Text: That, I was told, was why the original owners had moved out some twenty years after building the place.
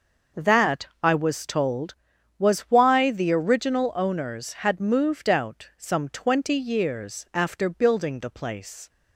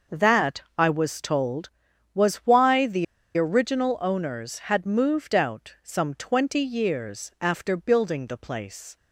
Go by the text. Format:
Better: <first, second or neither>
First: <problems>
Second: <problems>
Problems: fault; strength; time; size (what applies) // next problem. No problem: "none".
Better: first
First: none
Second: pauses between "the" and "original"; slight; at 3.0 s; 0.32 s long